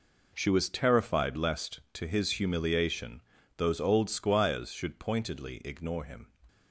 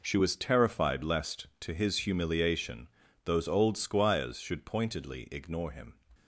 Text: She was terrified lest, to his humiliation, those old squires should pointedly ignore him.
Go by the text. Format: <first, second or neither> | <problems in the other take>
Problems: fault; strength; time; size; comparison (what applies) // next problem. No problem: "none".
neither | none